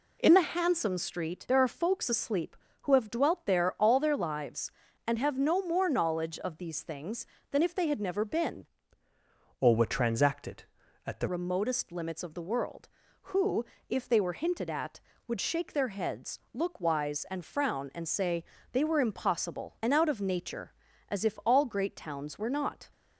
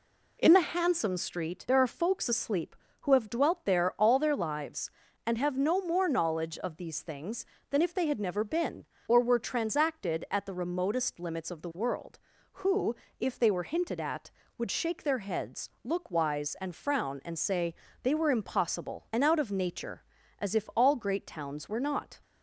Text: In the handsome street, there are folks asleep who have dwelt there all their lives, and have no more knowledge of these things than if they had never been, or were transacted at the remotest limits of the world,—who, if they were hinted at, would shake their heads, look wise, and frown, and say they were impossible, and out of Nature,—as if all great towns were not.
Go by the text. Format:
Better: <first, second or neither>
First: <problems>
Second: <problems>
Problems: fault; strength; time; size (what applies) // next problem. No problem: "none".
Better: second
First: changes voice from "or" to "the"; from 9.6 to 11.2 s; 1.6 s long // pauses between "say" and "they"; slight; at 18.4 s; 0.30 s long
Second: pauses between "say" and "they"; slight; at 17.7 s; 0.30 s long